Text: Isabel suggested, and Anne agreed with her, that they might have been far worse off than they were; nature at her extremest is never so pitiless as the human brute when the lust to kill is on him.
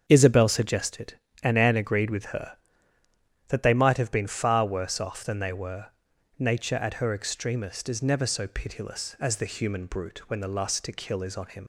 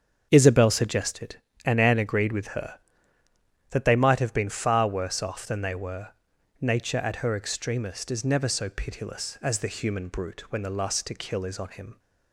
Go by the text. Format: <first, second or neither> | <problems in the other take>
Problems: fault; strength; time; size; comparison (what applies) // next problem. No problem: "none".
second | starts louder than the rest; strong; until 1.0 s; 7 dB; strong in the second // leaves "him" unfinished; at 11.6 s; 100 ms